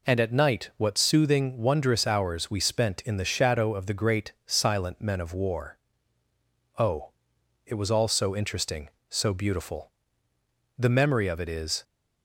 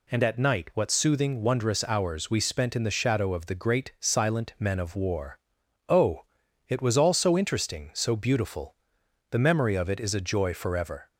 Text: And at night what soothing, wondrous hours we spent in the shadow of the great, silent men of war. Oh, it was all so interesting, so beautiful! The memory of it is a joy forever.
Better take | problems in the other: second | stops before "a joy forever"; at 11.8 s

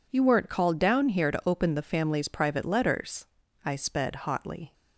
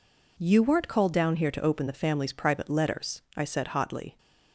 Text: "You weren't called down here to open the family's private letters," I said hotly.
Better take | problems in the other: second | says "sped" for "said"; at 3.7 s

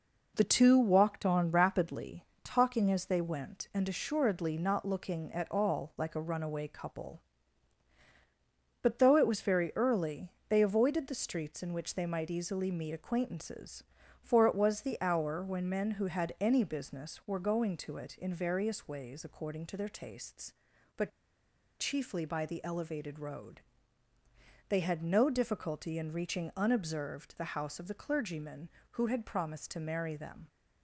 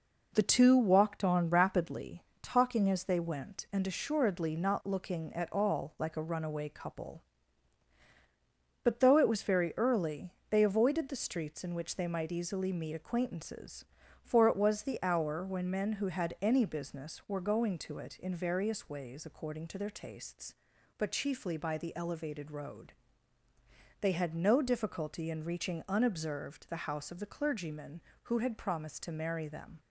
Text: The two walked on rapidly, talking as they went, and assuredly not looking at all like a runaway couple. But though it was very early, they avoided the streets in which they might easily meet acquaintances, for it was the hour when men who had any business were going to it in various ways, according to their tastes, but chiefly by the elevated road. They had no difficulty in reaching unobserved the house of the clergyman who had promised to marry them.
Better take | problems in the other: second | pauses between "but" and "chiefly"; noticeable; at 21.1 s; 0.69 s long

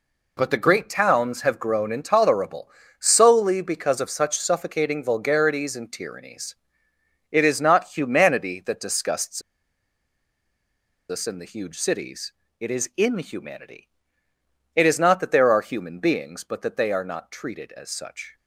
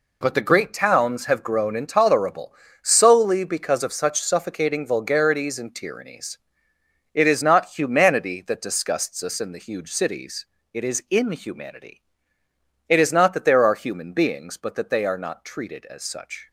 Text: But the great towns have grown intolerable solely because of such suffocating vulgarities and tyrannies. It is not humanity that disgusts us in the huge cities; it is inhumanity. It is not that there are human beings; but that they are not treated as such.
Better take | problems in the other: second | pauses between "intolerable" and "solely"; slight; at 2.7 s; 0.30 s long; slight in the second // pauses between "disgusts" and "us"; strong; at 9.4 s; 1.6 s long

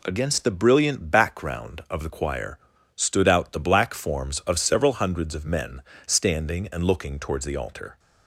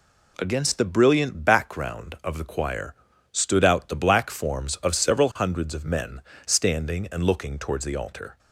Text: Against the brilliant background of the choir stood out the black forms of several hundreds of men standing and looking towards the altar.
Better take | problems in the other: neither | pauses between "choir" and "stood"; the same in both // pauses between "men" and "standing"; slight; the same in both

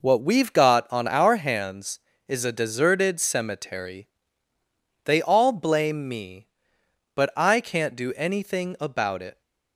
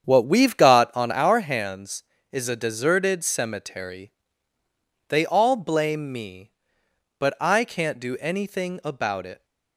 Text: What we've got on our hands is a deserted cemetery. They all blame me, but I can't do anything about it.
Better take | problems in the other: first | starts louder than the rest; strong; until 1.2 s; 8 dB

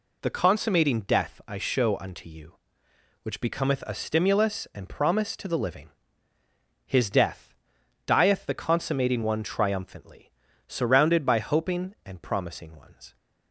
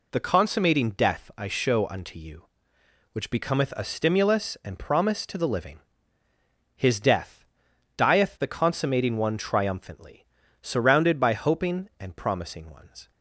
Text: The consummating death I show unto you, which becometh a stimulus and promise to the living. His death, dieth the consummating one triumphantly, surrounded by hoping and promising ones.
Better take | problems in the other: neither | none

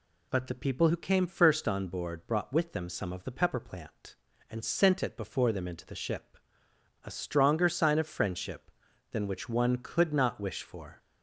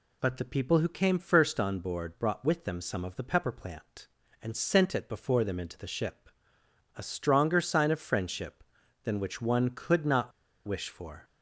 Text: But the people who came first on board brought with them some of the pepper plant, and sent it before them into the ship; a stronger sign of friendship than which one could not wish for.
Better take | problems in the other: first | pauses between "not" and "wish"; slight; at 10.3 s; 0.35 s long

